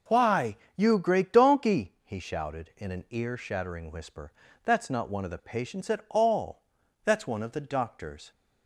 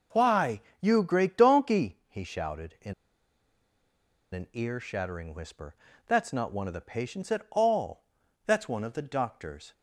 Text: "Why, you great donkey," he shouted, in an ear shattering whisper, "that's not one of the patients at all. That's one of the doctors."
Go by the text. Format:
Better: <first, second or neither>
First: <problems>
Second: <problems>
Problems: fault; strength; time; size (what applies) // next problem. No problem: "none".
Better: first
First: none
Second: pauses between "in" and "an"; strong; at 2.9 s; 1.4 s long